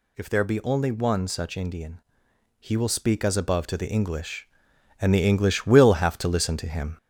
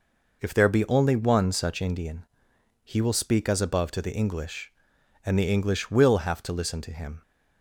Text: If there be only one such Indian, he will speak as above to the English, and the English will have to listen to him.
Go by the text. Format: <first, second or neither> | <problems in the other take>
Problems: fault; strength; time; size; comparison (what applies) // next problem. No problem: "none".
second | gets louder; noticeable; throughout; 4 dB